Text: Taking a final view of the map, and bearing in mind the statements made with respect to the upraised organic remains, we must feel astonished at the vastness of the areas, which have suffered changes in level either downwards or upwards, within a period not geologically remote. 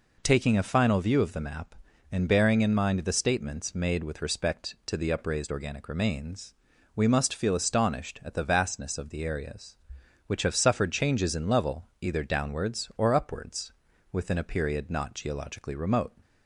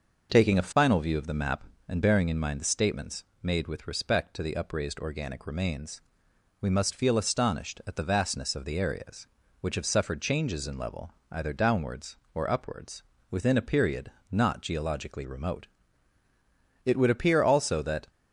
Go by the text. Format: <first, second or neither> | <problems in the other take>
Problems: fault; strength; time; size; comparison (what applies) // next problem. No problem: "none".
first | pauses between "statements" and "made"; slight; at 3.2 s; 0.22 s long // pauses between "level" and "either"; slight; at 11.1 s; 0.18 s long // pauses between "period" and "not"; slight; at 14.0 s; 0.22 s long // goes on to say "It would appear also that"; noticeable; from 16.8 s on; 1.2 s long